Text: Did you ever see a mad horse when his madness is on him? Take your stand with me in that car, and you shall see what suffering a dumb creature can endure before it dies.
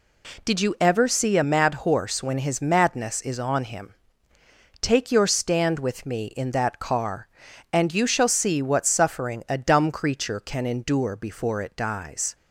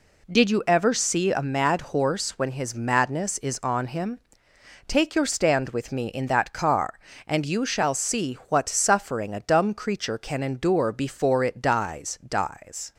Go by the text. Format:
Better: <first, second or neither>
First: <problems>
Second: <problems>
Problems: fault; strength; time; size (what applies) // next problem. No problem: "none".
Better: first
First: none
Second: says "dies" twice; at 12.2 s